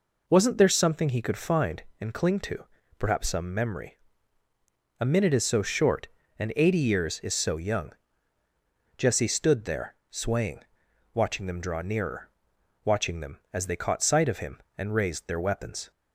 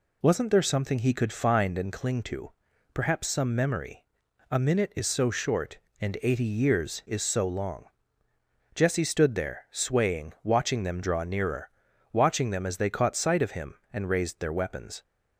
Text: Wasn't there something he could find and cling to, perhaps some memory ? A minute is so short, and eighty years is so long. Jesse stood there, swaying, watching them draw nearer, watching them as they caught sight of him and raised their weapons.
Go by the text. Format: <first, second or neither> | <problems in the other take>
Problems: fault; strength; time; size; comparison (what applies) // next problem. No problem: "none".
second | says "young" for "long"; at 7.5 s